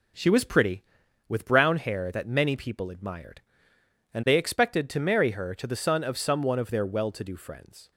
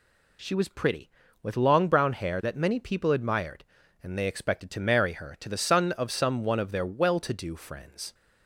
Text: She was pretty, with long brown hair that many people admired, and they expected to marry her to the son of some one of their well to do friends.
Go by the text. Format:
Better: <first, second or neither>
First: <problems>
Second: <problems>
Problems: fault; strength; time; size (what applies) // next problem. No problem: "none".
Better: second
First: skips "long"; at 1.4 s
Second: none